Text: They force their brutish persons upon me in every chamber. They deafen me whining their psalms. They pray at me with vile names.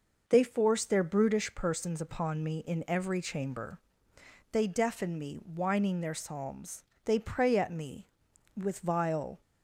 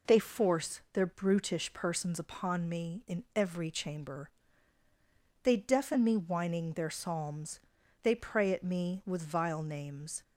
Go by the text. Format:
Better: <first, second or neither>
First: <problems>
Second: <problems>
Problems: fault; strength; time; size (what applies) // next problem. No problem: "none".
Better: second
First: stops before "names"; at 9.4 s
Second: none